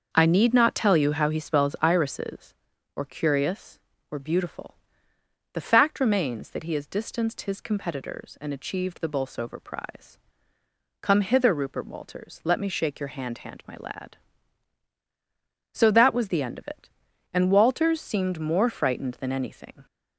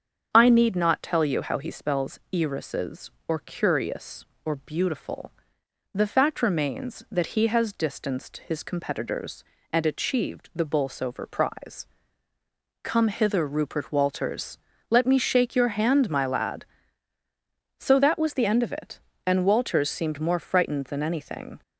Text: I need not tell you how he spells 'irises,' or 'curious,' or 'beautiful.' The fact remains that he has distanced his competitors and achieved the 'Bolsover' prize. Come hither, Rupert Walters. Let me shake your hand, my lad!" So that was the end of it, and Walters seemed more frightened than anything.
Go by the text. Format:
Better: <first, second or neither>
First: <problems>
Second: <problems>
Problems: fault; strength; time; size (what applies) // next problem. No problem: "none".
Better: second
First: starts louder than the rest; until 1.1 s; 6 dB // says "hand" twice; at 13.3 s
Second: starts louder than the rest; strong; until 1.3 s; 7 dB